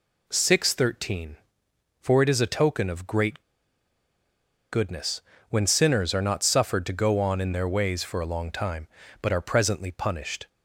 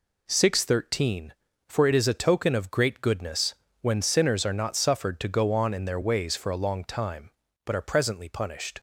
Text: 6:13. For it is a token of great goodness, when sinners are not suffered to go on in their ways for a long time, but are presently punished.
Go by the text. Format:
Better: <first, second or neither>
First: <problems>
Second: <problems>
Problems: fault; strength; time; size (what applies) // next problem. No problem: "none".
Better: second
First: pauses between "great" and "goodness"; strong; at 3.4 s; 1.3 s long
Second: none